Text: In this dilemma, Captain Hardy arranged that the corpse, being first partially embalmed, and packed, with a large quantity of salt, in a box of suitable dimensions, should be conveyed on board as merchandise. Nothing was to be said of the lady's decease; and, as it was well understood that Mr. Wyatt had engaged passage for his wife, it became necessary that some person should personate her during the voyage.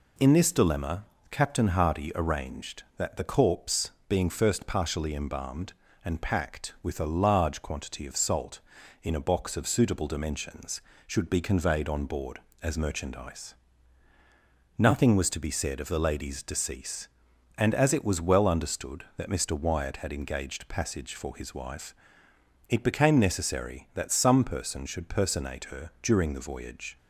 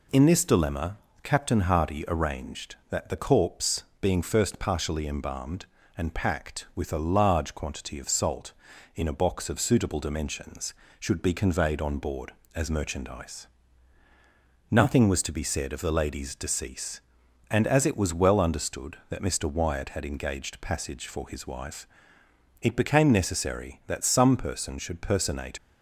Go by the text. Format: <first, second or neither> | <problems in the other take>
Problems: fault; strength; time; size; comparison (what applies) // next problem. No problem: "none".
first | stops before "her during the voyage"; at 25.5 s